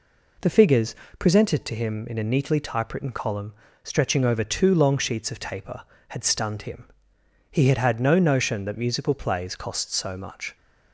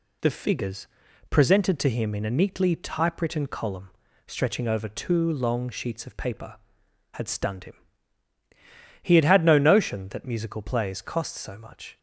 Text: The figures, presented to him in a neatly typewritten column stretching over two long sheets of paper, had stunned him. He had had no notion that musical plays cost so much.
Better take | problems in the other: second | pauses between "column" and "stretching"; slight; at 3.5 s; 0.32 s long; slight in the second // says "taper" for "paper"; at 5.3 s

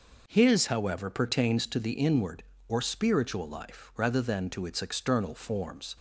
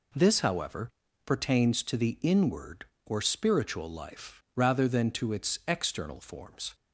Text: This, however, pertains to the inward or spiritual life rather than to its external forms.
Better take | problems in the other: second | says "His" for "This"; at 0.2 s

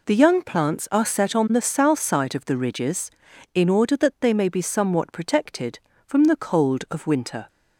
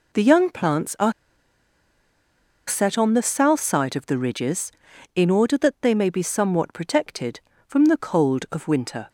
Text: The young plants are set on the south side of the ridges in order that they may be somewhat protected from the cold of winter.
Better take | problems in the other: first | pauses between "are" and "set"; strong; at 1.1 s; 1.5 s long

